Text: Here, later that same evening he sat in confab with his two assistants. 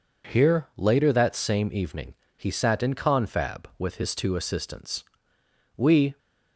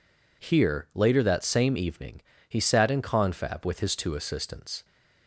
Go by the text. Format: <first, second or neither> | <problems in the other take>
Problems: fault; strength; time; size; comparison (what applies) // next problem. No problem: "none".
second | pauses between "evening" and "he"; slight; at 2.1 s; 0.23 s long; slight in the second // goes on to say "We"; slight; from 5.7 s on; 0.40 s long